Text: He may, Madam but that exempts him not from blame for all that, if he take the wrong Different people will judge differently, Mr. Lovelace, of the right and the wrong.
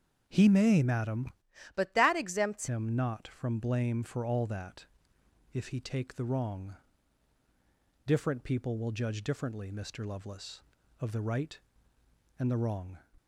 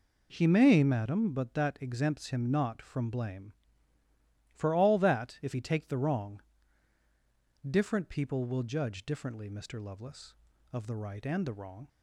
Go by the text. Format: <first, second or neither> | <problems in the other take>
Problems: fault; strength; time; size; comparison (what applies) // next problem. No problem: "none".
second | starts louder than the rest; until 1.2 s; 7 dB // changes voice from "but" to "exempts"; from 1.7 to 2.6 s; 0.9 s long // pauses between "wrong" and "Different"; strong; at 6.7 s; 1.3 s long; also in the second